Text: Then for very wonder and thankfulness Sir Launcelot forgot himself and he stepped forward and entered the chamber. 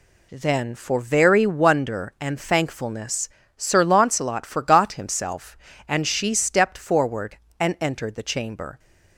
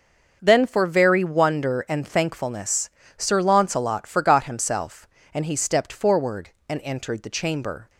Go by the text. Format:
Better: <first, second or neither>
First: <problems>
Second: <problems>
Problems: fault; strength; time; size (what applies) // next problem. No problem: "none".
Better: second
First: pauses between "thankfulness" and "Sir"; slight; at 3.2 s; 0.28 s long // says "she" for "he"; at 6.0 s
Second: pauses between "thankfulness" and "Sir"; slight; at 2.8 s; 0.28 s long